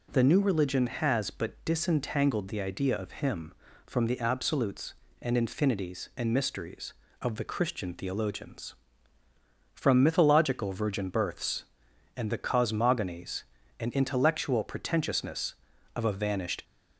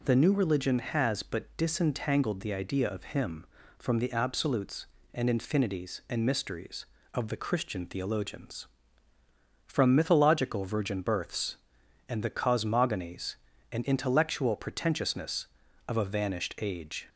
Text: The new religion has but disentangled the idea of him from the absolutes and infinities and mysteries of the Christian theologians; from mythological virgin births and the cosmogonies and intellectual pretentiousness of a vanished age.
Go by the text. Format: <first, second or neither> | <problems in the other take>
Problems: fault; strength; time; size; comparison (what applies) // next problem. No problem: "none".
second | stops before "age"; at 16.6 s